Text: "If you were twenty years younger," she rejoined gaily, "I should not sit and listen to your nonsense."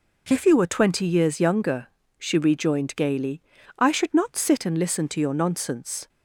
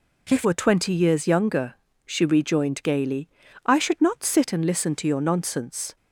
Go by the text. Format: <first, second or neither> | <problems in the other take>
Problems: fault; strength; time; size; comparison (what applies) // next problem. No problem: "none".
first | skips "you"; at 0.4 s